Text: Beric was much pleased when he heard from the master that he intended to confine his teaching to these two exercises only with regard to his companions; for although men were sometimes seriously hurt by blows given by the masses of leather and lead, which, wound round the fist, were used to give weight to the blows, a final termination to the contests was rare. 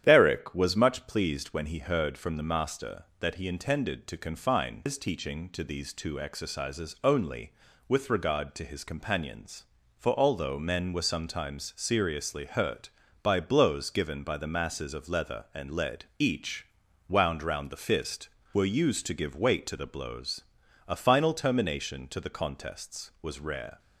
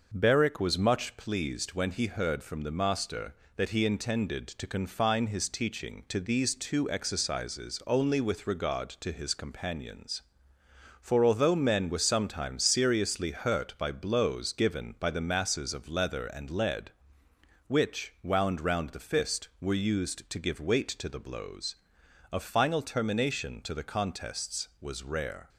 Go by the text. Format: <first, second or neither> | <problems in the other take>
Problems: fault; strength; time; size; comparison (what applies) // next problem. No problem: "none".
second | starts louder than the rest; strong; until 1.0 s; 10 dB // says "each" for "which"; at 16.1 s